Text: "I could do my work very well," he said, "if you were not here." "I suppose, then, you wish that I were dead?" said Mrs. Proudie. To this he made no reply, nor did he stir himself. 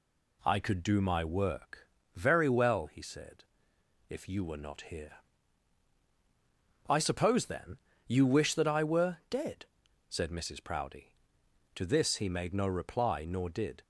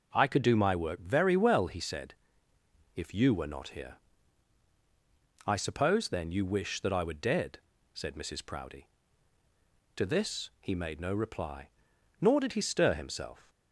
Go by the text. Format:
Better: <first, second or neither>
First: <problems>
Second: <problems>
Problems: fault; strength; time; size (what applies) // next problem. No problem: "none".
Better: second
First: pauses between "work" and "very"; slight; at 1.8 s; 0.26 s long // stops before "he stir himself"; at 13.8 s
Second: none